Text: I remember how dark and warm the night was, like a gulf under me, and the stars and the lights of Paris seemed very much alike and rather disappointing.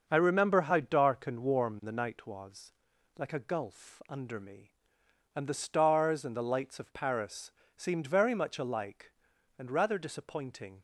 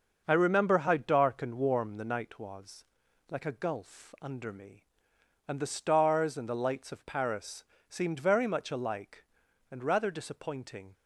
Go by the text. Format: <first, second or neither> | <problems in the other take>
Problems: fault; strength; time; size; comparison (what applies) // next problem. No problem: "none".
neither | starts louder than the rest; the same in both // pauses between "Paris" and "seemed"; slight; the same in both